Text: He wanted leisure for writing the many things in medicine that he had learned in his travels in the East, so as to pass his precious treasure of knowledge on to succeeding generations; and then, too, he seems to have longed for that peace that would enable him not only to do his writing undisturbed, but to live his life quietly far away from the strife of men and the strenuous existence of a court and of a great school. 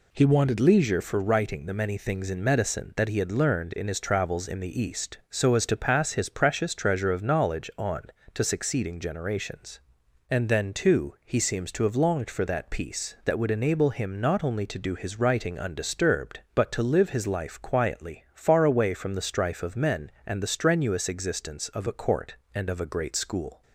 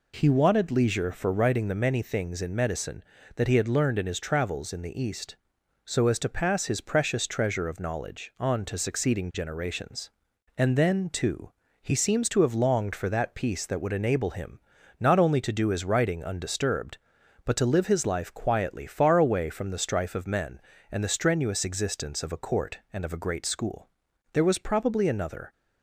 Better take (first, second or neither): first